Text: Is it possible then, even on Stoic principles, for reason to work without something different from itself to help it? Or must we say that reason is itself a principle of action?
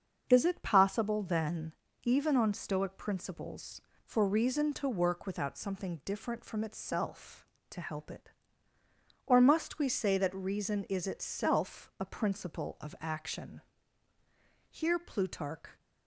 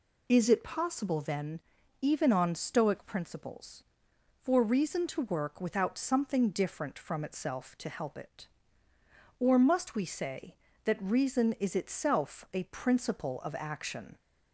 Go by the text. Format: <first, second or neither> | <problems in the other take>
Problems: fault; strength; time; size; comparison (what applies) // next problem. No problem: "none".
second | starts louder than the rest; until 1.3 s; 7 dB // goes on to say "Here Plutarch"; noticeable; from 14.6 s on; 1.1 s long